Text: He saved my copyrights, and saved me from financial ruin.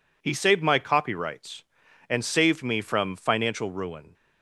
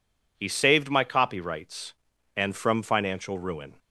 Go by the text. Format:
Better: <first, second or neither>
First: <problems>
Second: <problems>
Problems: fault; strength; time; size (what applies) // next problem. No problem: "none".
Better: first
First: none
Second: skips "saved me"; at 2.5 s